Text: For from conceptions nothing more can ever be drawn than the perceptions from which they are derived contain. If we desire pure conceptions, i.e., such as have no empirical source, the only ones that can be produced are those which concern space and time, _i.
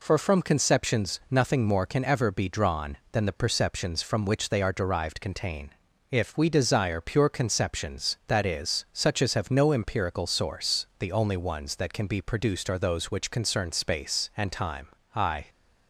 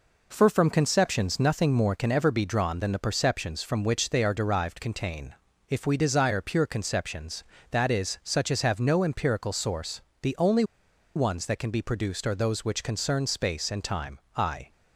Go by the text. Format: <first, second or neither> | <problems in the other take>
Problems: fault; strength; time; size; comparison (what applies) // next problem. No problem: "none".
first | pauses between "only" and "ones"; noticeable; at 10.6 s; 0.52 s long